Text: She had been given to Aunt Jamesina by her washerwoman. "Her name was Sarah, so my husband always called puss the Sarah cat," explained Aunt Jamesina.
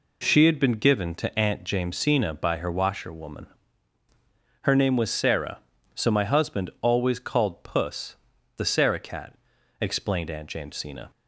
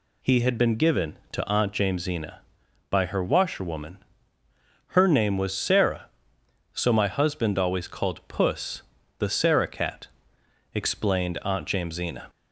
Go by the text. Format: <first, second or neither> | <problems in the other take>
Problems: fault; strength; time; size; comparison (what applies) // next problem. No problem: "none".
first | says "He" for "She"; at 0.2 s // pauses between "puss" and "the"; slight; at 8.8 s; 0.34 s long; also in the first